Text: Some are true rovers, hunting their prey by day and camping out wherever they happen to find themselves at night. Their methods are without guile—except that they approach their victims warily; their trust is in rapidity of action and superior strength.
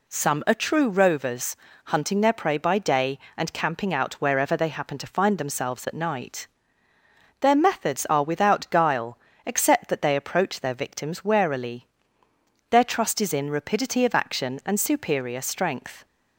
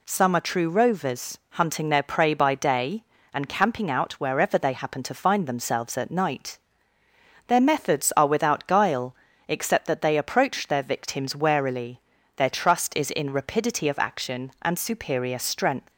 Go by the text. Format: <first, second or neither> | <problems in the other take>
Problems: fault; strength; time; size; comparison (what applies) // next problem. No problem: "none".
neither | none